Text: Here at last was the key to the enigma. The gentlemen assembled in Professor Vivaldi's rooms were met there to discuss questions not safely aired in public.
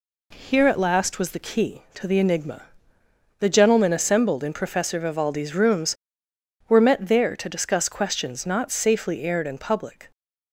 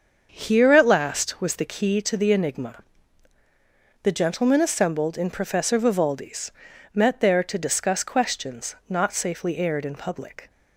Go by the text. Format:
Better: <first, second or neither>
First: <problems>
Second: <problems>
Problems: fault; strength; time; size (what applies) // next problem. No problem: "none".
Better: first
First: none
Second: starts louder than the rest; until 1.3 s; 6.5 dB // skips "rooms were"; at 6.7 s